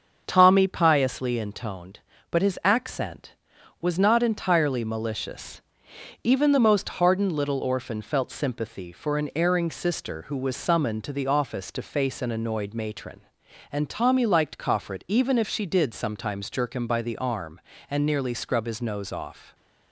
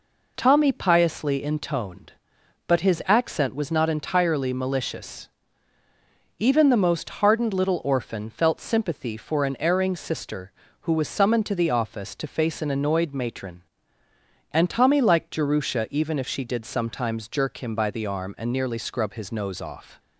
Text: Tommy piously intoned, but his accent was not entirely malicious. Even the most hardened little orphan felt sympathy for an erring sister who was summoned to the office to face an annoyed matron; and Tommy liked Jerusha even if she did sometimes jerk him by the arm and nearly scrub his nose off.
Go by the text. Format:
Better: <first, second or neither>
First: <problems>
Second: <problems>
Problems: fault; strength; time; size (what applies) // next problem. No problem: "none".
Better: second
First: starts louder than the rest; until 1.2 s; 7 dB // says "Coffret" for "Jerusha"; at 14.5 s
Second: none